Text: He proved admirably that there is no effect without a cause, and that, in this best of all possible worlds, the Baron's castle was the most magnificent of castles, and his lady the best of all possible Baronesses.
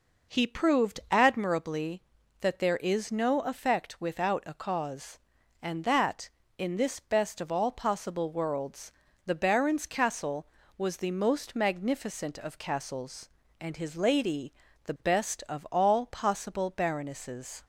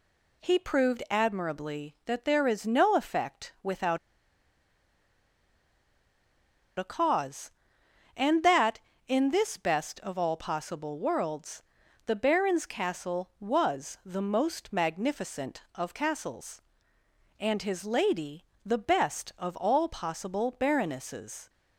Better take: first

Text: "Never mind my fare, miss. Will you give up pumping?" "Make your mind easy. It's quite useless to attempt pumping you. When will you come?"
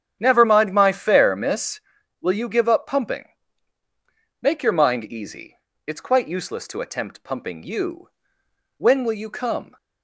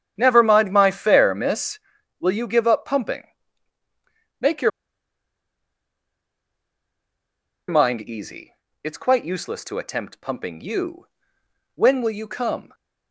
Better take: first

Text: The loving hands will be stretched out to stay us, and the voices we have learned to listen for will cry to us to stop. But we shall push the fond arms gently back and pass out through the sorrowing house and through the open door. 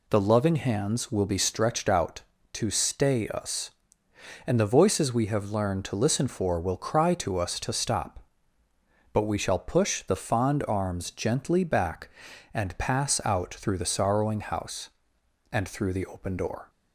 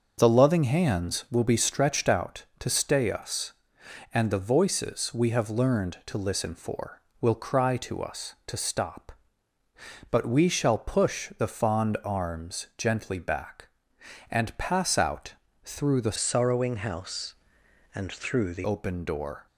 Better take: first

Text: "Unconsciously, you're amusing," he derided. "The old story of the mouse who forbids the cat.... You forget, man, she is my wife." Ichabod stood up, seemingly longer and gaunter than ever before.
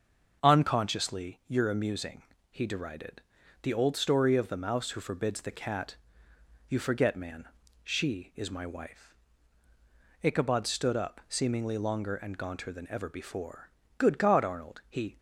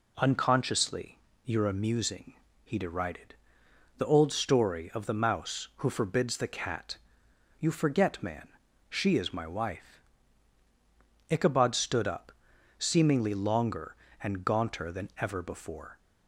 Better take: second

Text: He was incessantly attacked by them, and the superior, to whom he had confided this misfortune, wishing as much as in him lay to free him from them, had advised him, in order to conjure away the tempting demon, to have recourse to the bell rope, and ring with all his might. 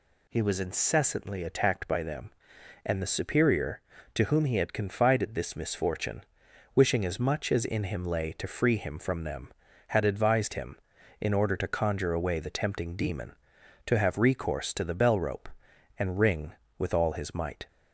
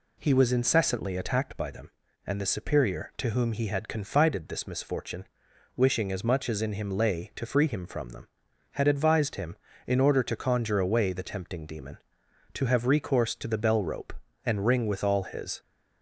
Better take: first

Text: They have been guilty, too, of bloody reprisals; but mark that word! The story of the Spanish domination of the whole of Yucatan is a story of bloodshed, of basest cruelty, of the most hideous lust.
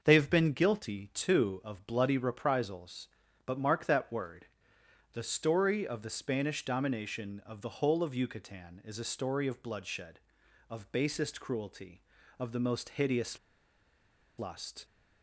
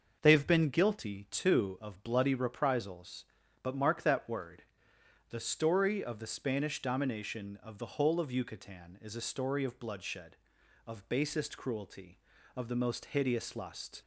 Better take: second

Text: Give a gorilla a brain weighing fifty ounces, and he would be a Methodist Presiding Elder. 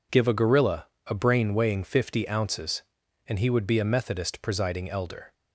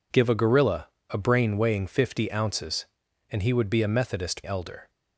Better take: first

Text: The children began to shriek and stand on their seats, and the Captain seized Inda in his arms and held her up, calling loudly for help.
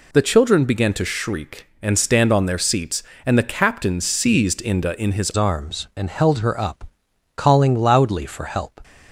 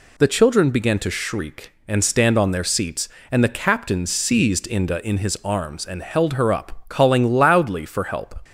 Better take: second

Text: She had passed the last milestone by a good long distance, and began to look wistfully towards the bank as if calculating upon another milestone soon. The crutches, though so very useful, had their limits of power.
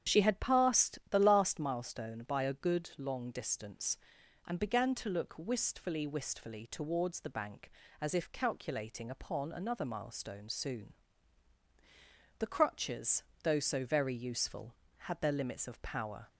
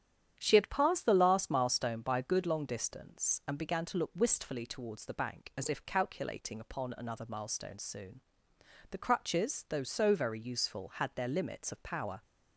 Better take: second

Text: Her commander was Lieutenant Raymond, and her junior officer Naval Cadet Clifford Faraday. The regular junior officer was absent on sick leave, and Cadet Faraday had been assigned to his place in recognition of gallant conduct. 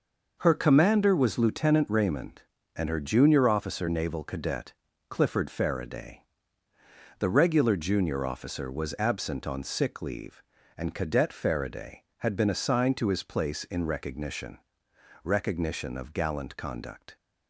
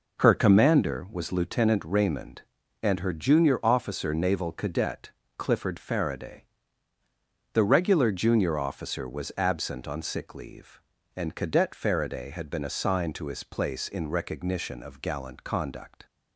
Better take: second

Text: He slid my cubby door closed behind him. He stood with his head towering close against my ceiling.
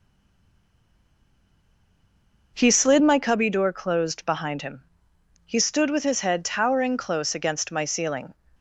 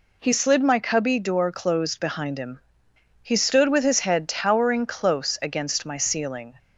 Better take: second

